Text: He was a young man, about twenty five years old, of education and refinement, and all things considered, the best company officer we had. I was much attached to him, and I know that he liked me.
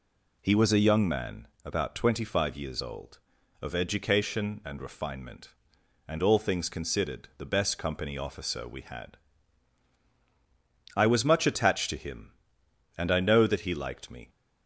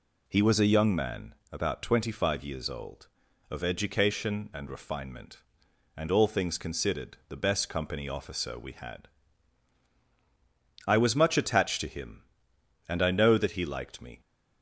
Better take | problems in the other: neither | none

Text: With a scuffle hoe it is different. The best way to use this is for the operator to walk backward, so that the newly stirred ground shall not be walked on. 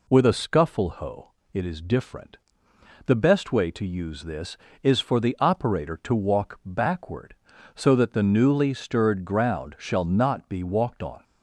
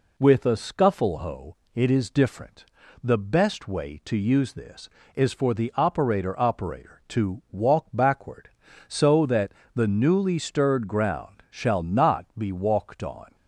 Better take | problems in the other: first | pauses between "hoe" and "it"; slight; at 1.5 s; 0.16 s long; slight in the first // says "operator" twice; at 6.3 s // pauses between "that" and "the"; slight; at 9.5 s; 0.24 s long

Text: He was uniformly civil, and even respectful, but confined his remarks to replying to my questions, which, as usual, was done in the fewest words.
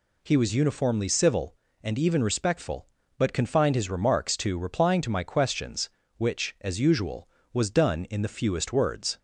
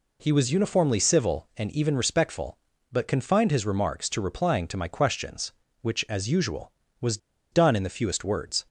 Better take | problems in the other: first | pauses between "was" and "done"; slight; at 7.1 s; 0.34 s long

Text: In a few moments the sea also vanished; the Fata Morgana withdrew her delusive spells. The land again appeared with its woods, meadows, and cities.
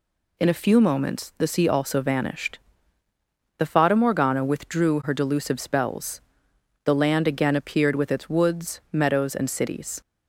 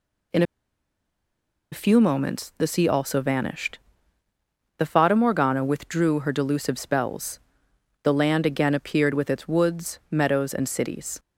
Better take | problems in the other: first | pauses between "In" and "a"; strong; at 0.4 s; 1.2 s long

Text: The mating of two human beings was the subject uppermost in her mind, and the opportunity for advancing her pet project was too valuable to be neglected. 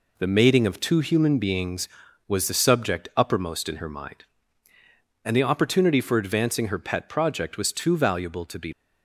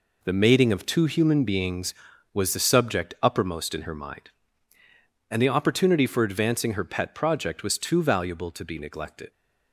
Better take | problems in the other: second | stops before "neglected"; at 8.7 s

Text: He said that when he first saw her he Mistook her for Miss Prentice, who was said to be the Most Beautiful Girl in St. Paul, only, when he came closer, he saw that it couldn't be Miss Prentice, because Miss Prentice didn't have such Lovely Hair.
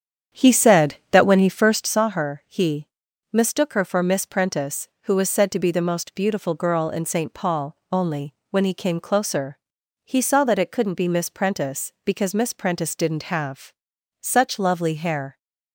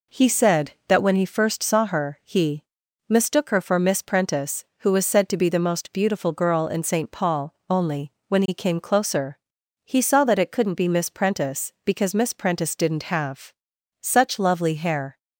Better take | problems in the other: second | starts louder than the rest; strong; until 2.0 s; 8.5 dB // pauses between "he" and "Mistook"; noticeable; at 2.8 s; 0.48 s long; noticeable in the second // pauses between "have" and "such"; noticeable; at 13.7 s; 0.48 s long; noticeable in the second

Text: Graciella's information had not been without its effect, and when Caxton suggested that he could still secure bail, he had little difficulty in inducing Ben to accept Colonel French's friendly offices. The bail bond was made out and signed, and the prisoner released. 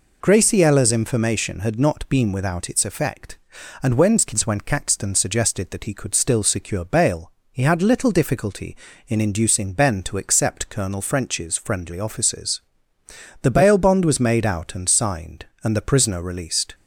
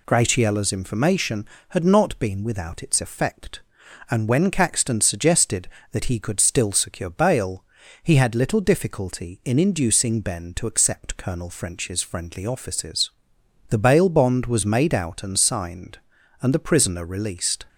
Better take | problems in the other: second | says "when" twice; at 4.4 s

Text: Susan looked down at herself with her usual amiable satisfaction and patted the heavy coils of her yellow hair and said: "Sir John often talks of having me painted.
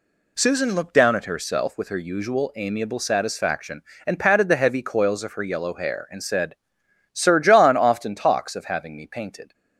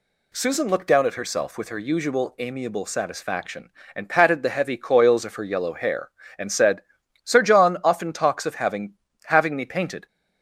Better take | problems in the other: first | says "having" twice; at 9.2 s

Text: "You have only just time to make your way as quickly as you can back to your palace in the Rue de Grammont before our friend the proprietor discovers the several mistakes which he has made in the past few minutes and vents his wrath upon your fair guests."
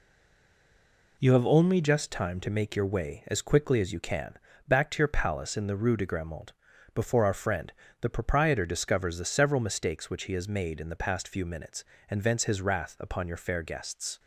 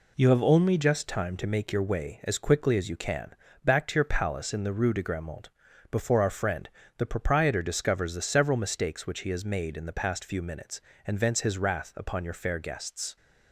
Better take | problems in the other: second | stays silent before the first word; noticeable; until 1.1 s; 1.1 s long // pauses between "can" and "back"; slight; at 4.3 s; 0.30 s long; slight in the second // pauses between "Grammont" and "before"; at 6.5 s; 0.40 s long; also in the second // pauses between "friend" and "the"; slight; at 7.7 s; 0.30 s long; slight in the second

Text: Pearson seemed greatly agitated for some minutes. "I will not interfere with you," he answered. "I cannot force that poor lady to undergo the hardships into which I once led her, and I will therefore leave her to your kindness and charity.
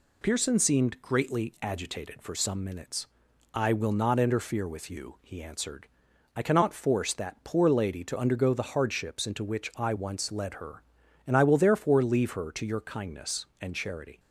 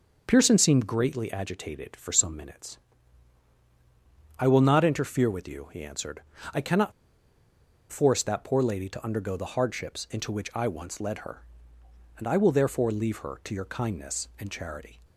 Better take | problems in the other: first | starts louder than the rest; noticeable; until 1.2 s; 6 dB // pauses between "cannot" and "force"; at 6.9 s; 1.0 s long

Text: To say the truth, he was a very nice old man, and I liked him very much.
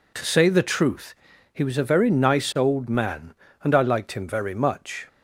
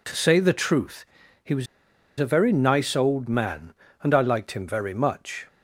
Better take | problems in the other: first | pauses between "was" and "a"; noticeable; at 1.6 s; 0.53 s long

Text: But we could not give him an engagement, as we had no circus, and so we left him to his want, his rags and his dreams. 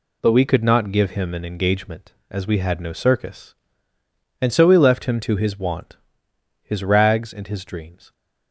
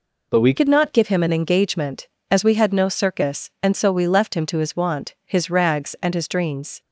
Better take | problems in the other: first | changes voice at "could"; from 0.5 s on; 6.3 s long

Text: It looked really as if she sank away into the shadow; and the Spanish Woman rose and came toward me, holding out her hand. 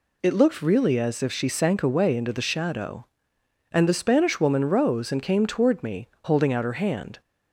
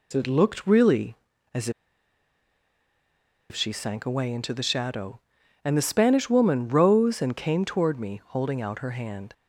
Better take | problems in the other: first | pauses between "as" and "if"; strong; at 1.6 s; 1.8 s long

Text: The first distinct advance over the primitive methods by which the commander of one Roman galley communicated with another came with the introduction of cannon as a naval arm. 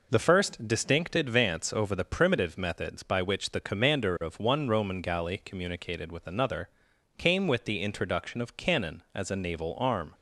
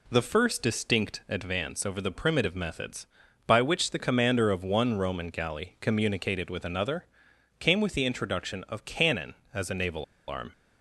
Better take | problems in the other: first | pauses between "another" and "came"; noticeable; at 7.0 s; 0.54 s long; noticeable in the first // pauses between "naval" and "arm"; slight; at 10.0 s; 0.23 s long

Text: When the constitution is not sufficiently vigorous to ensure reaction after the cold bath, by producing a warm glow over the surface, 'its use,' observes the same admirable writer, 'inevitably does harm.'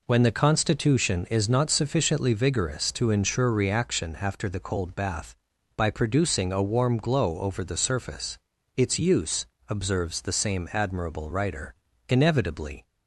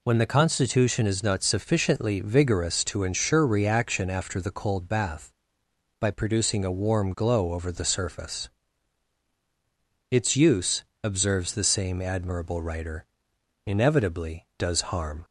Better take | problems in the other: second | stops before "does harm"; at 12.8 s

